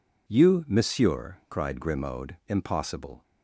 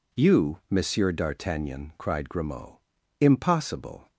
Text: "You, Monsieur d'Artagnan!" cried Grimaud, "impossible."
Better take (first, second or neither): second